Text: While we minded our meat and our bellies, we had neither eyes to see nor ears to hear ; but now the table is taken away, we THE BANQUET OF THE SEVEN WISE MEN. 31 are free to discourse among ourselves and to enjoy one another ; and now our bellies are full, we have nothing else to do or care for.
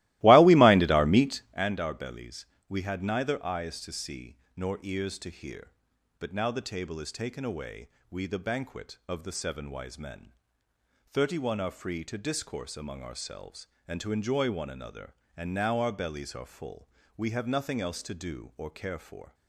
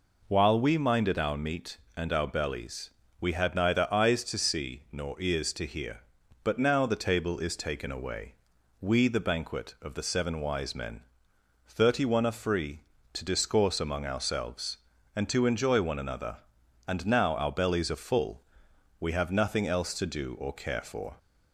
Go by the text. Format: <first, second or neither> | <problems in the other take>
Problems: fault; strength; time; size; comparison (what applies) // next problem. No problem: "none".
second | starts louder than the rest; strong; until 1.6 s; 18 dB // pauses between "see" and "nor"; slight; at 4.3 s; 0.20 s long